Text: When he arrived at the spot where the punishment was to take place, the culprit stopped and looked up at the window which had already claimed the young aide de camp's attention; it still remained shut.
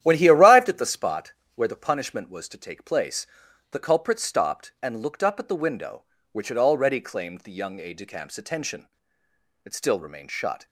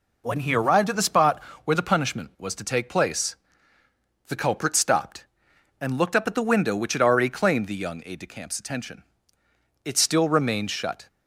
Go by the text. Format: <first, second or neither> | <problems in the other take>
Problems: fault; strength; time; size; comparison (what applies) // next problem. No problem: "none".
second | starts louder than the rest; strong; until 1.1 s; 11.5 dB // pauses between "spot" and "where"; slight; at 1.3 s; 0.24 s long; slight in the second